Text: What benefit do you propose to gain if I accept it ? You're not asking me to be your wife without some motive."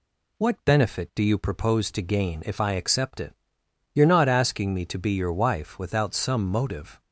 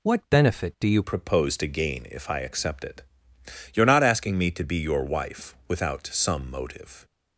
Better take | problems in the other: first | changes voice at "propose"; from 1.0 s on; 6.0 s long

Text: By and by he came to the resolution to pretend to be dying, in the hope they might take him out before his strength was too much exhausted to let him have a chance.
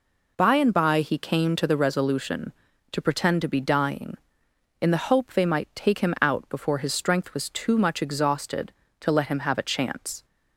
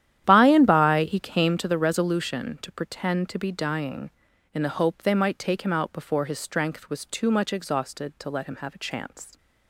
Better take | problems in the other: first | starts louder than the rest; strong; until 1.7 s; 11 dB

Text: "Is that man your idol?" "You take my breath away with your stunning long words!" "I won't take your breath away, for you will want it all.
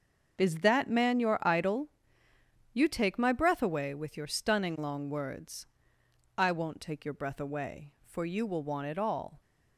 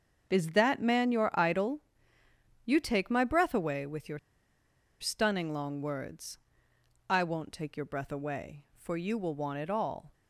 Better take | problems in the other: first | starts louder than the rest; strong; until 1.4 s; 7 dB; also in the first // pauses between "your" and "stunning"; noticeable; at 4.1 s; 0.83 s long

